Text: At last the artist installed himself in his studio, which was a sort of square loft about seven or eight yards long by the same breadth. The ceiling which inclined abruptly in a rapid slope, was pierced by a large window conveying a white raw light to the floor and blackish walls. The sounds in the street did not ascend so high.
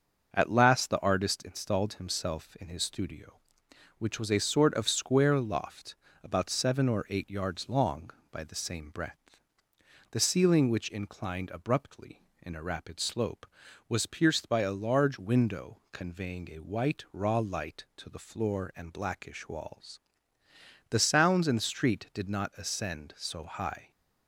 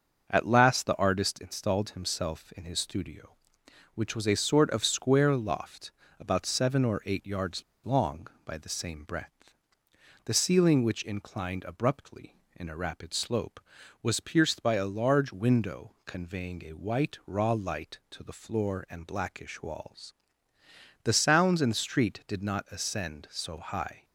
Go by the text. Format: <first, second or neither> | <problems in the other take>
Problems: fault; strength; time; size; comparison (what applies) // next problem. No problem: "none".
first | starts louder than the rest; until 1.3 s; 6.5 dB; also in the first // pauses between "loft" and "about"; slight; at 5.9 s; 0.28 s long; slight in the first // pauses between "yards" and "long"; slight; at 7.6 s; 0.23 s long